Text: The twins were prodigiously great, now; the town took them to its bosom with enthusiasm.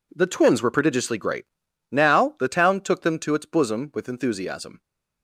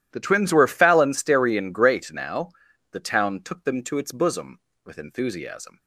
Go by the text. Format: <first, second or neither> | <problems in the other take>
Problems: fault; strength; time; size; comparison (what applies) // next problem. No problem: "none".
first | says "phalansterian" for "prodigiously"; at 0.6 s